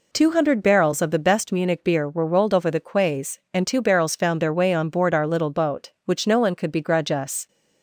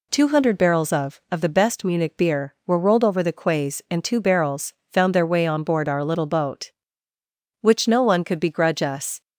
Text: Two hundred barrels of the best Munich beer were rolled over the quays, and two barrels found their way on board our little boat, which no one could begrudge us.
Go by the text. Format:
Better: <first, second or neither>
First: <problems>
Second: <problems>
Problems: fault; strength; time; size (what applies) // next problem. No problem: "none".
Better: first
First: none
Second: says "of" twice; at 1.3 s // pauses between "barrels" and "found"; slight; at 4.7 s; 0.18 s long